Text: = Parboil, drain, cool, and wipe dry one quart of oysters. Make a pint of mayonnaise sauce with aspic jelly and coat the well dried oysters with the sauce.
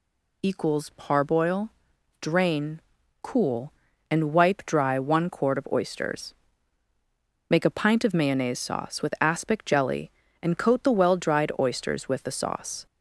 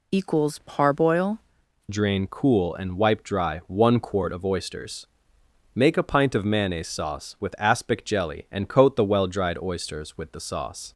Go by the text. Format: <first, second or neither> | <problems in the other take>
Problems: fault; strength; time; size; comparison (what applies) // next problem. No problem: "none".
first | changes voice at "drain"; from 1.8 s on; 9.1 s long